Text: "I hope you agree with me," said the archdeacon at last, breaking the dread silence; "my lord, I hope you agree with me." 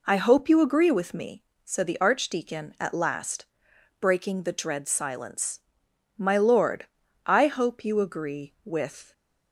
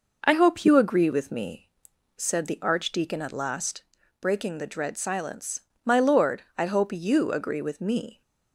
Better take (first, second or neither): second